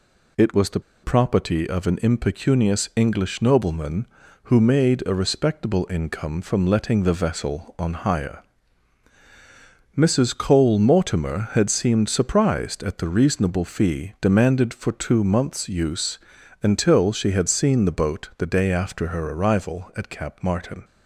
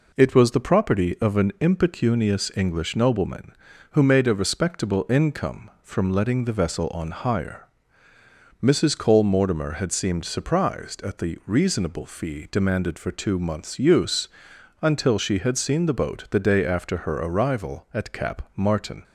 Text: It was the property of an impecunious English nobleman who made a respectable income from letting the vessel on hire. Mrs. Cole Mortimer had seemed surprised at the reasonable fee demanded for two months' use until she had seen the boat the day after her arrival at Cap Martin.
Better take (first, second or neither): second